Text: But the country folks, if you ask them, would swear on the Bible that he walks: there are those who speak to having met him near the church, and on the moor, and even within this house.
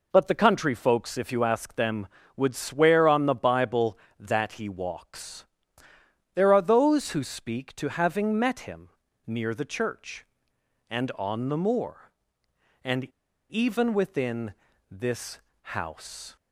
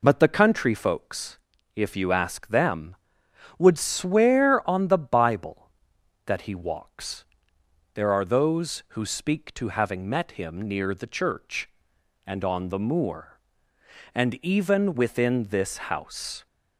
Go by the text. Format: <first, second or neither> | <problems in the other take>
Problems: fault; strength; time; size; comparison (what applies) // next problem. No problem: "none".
second | pauses between "him" and "near"; slight; at 8.8 s; 0.36 s long // pauses between "and" and "even"; noticeable; at 13.0 s; 0.46 s long // pauses between "within" and "this"; slight; at 14.5 s; 0.34 s long // pauses between "this" and "house"; at 15.3 s; 0.38 s long; slight in the second